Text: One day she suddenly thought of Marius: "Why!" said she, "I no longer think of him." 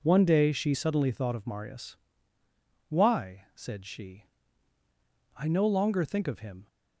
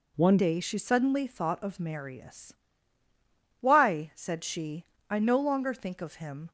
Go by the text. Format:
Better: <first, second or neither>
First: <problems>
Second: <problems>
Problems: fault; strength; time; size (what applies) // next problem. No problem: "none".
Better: first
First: none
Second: changes voice at "day"; from 0.3 s on; 6.2 s long